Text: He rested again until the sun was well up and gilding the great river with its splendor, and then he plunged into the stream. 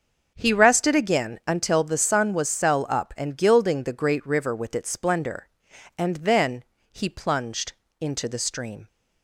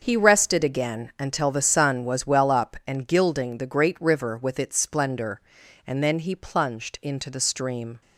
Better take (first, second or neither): second